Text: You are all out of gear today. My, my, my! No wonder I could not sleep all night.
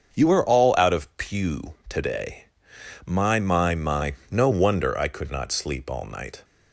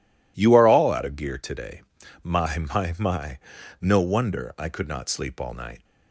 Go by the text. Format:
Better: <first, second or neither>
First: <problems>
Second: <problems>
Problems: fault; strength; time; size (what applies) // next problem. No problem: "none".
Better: second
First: starts louder than the rest; until 1.1 s; 6.5 dB // says "pew" for "gear"; at 1.1 s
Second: none